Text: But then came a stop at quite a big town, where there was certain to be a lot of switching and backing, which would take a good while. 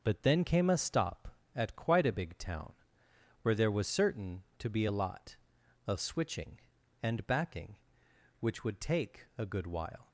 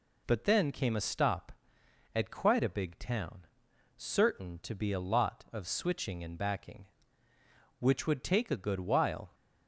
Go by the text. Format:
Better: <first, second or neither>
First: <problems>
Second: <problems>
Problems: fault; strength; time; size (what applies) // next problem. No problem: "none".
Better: first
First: none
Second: skips "where there was"; at 3.7 s